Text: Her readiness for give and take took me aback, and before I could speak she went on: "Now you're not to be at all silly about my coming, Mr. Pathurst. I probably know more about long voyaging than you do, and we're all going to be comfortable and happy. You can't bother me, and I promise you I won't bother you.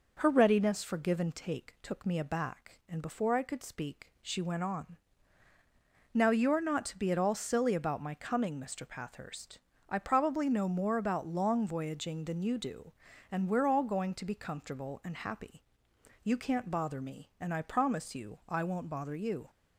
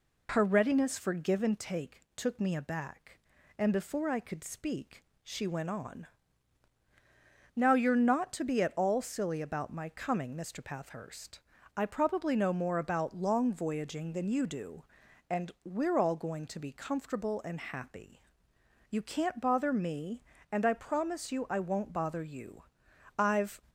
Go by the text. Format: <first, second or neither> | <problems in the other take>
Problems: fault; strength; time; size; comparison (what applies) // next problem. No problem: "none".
first | pauses between "speak" and "she"; slight; at 5.0 s; 0.22 s long // goes on to say "I've"; slight; from 23.1 s on; 0.42 s long